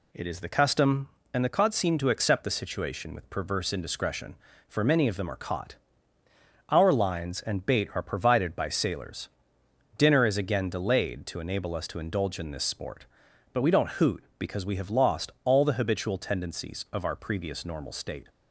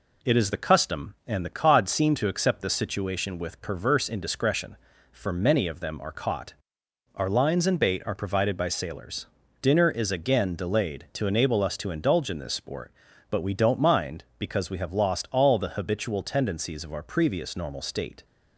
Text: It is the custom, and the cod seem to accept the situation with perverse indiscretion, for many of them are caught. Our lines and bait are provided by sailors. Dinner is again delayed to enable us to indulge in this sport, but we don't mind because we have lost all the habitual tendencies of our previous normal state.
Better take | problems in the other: second | says "hoot" for "mind"; at 13.9 s

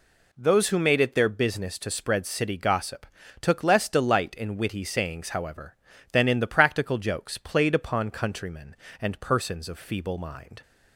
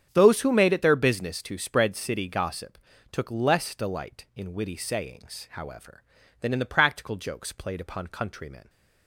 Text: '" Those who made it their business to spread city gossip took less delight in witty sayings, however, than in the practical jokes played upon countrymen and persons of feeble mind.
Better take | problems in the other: first | starts louder than the rest; strong; until 1.1 s; 8 dB // pauses between "gossip" and "took"; slight; at 2.7 s; 0.32 s long; slight in the first // stops before "and persons of feeble mind"; at 8.6 s

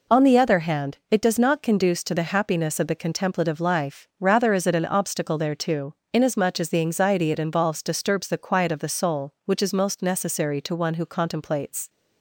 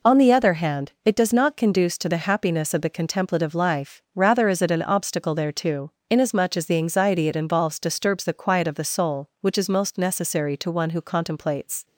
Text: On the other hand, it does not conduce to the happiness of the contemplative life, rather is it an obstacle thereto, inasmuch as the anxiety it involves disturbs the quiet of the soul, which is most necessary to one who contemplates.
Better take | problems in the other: neither | none

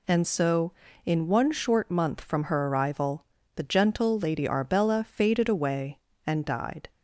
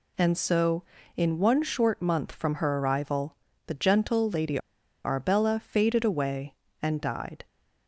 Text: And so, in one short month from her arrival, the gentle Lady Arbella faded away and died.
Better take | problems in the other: first | pauses between "Lady" and "Arbella"; at 4.5 s; 0.44 s long

